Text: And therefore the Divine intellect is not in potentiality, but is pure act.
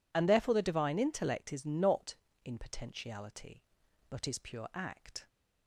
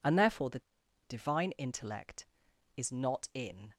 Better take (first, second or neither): first